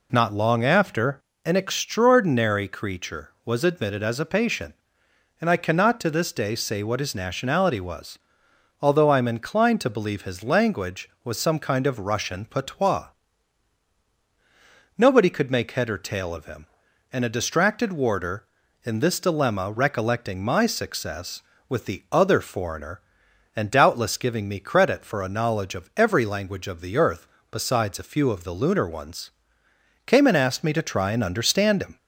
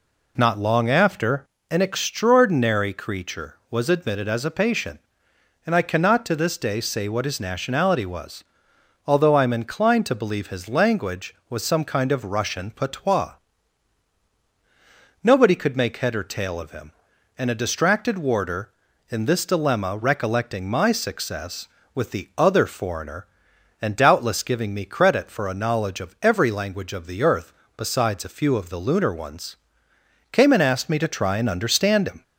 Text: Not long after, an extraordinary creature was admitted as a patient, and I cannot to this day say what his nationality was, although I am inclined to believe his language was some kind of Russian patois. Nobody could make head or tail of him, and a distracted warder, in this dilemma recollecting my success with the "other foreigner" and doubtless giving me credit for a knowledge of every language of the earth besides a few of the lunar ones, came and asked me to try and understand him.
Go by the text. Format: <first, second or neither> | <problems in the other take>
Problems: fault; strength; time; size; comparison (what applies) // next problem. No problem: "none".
neither | pauses between "earth" and "besides"; slight; the same in both